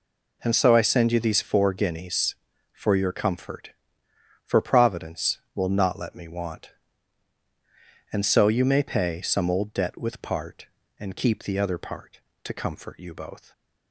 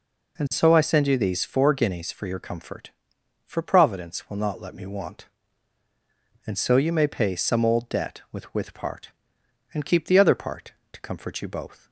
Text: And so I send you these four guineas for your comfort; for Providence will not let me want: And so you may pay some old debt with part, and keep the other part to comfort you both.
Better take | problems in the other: first | says "with" twice; at 8.5 s

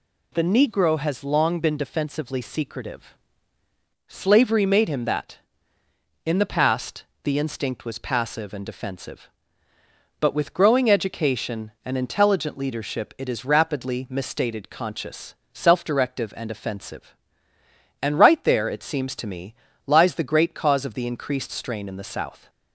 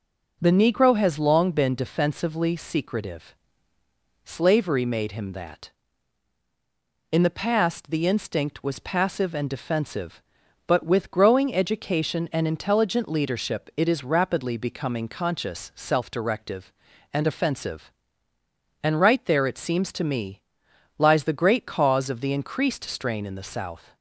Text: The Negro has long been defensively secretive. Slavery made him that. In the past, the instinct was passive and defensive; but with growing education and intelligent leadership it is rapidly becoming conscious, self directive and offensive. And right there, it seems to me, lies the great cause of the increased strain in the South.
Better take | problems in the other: second | says "misstated" for "becoming"; at 14.0 s

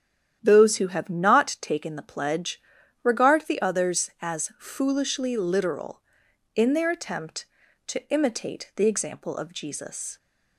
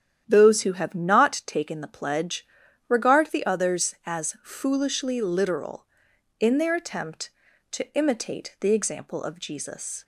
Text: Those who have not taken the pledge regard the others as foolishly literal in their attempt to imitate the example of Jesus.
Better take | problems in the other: neither | starts louder than the rest; strong; the same in both // pauses between "pledge" and "regard"; the same in both

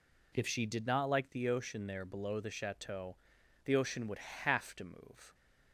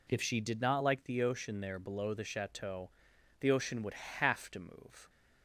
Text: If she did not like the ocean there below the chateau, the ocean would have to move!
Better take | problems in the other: neither | none

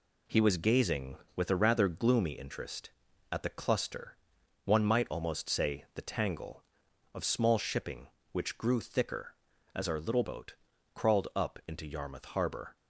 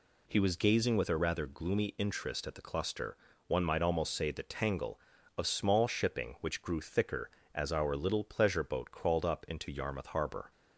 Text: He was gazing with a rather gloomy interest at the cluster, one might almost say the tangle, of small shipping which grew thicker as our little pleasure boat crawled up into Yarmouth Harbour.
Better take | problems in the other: second | skips "pleasure"; at 10.2 s // pauses between "boat" and "crawled"; at 10.5 s; 0.40 s long

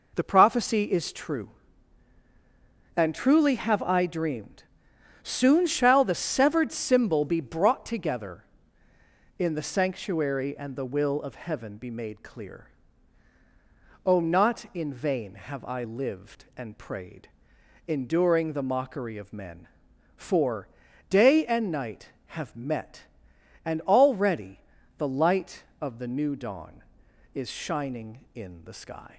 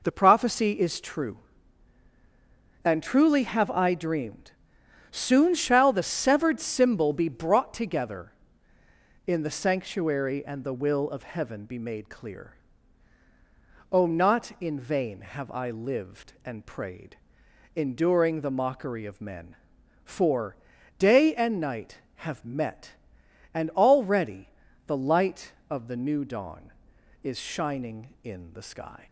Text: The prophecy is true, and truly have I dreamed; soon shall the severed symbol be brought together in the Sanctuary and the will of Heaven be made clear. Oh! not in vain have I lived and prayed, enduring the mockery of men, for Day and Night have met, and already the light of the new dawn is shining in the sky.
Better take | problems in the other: neither | pauses between "for" and "Day"; the same in both // pauses between "already" and "the"; the same in both

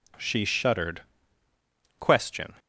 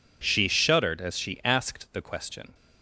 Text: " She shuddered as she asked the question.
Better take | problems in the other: second | skips "as she asked the"; at 1.4 s

